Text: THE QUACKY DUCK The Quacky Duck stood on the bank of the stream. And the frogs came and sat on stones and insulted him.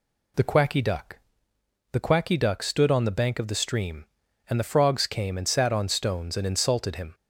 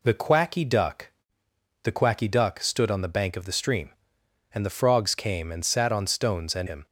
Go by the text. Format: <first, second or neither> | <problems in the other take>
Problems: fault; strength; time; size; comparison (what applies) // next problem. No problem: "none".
first | pauses between "DUCK" and "The"; noticeable; at 1.1 s; 0.72 s long; noticeable in the first // skips "insulted"; at 6.6 s